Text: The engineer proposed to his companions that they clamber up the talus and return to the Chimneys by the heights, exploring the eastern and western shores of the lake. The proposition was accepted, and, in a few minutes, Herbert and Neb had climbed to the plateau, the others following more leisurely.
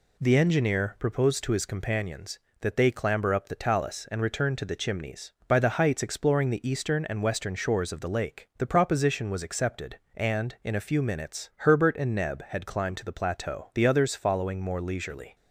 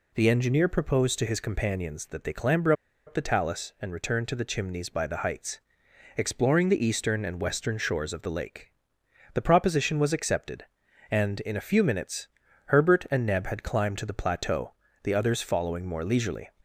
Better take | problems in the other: first | pauses between "clamber" and "up"; slight; at 2.7 s; 0.34 s long

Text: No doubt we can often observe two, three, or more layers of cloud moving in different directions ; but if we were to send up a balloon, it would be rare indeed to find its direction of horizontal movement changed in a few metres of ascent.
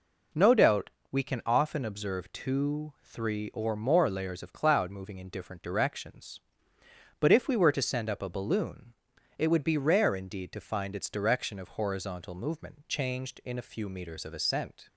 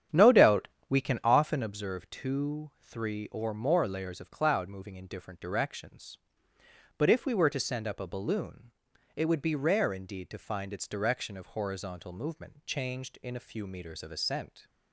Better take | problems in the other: first | starts louder than the rest; strong; until 1.8 s; 9.5 dB // pauses between "doubt" and "we"; slight; at 0.6 s; 0.20 s long; slight in the first

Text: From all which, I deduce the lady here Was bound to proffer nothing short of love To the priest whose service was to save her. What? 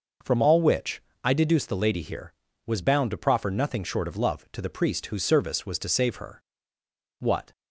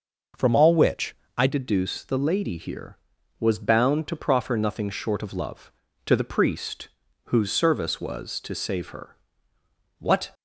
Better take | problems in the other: first | changes voice at "deduce"; from 1.4 s on; 8.9 s long // pauses between "priest" and "whose"; at 6.8 s; 0.40 s long

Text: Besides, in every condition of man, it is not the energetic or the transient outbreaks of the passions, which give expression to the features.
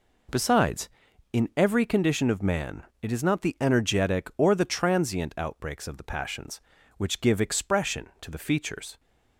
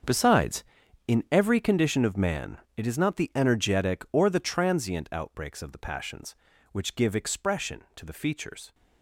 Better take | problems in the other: first | gets quieter; strong; throughout; 16 dB

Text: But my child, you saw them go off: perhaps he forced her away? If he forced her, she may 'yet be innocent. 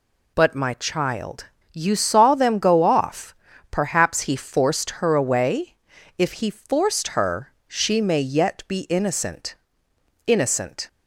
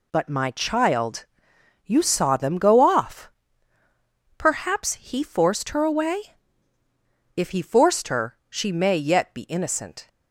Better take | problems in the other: second | says "innocent" twice; at 10.2 s

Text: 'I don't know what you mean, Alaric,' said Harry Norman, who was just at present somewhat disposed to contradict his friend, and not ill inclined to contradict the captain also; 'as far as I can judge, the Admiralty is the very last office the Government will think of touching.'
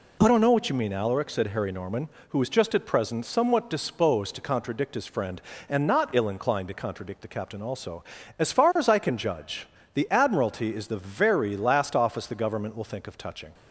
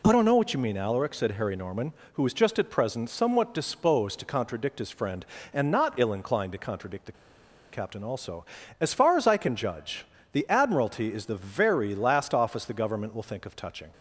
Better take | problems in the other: first | pauses between "the" and "captain"; noticeable; at 7.1 s; 0.59 s long

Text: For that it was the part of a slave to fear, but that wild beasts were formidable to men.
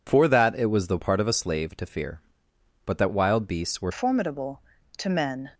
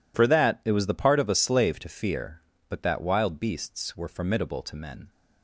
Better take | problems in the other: second | changes voice at "formidable"; from 3.9 s on; 1.5 s long

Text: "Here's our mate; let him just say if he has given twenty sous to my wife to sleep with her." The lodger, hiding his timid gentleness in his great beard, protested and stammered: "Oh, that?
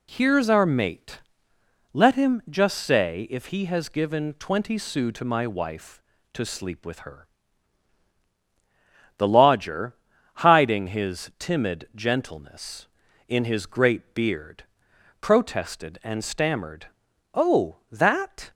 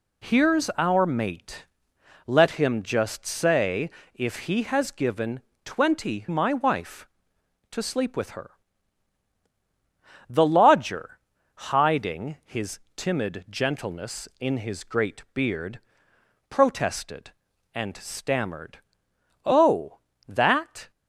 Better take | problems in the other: first | pauses between "say" and "if"; slight; at 3.9 s; 0.24 s long // pauses between "given" and "twenty"; slight; at 5.4 s; 0.24 s long // skips "sous to"; at 6.2 s // pauses between "his" and "timid"; slight; at 12.7 s; 0.16 s long

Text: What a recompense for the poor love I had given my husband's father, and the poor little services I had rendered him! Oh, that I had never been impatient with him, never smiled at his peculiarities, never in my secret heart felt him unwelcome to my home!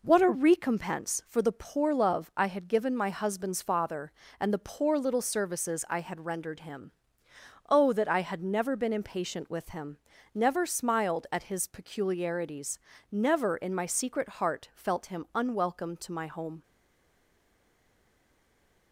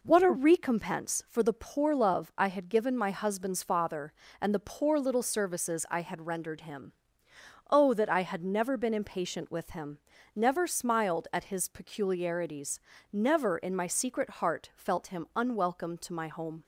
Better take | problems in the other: second | stays silent after the last word; from 16.6 s on; 2.3 s long

